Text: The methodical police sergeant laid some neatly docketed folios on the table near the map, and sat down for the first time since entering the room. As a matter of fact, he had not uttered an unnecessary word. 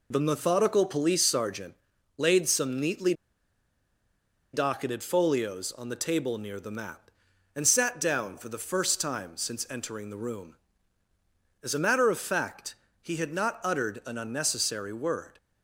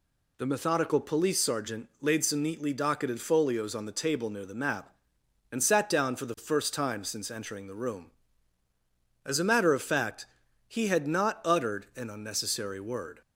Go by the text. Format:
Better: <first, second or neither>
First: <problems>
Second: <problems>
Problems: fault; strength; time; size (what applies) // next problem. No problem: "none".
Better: second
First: pauses between "sergeant" and "laid"; at 1.7 s; 0.44 s long // pauses between "neatly" and "docketed"; strong; at 3.1 s; 1.4 s long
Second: none